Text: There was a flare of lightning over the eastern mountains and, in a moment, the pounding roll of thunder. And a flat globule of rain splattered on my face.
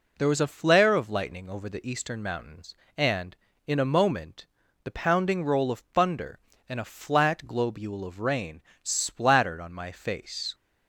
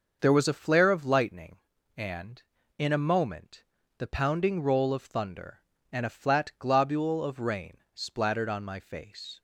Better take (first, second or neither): first